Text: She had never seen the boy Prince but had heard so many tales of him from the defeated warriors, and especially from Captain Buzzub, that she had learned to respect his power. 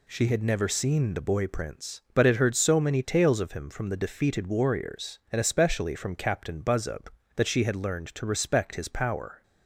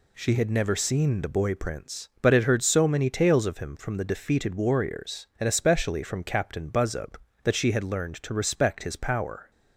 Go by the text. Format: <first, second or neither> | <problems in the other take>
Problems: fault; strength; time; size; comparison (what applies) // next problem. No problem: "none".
neither | none